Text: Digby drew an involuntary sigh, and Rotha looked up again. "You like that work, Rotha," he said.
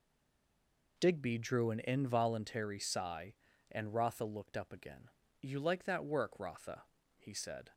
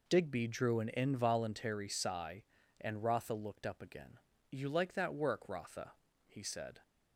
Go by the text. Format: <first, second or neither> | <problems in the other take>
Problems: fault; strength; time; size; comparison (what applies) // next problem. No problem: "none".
second | stays silent before the first word; until 0.9 s; 0.9 s long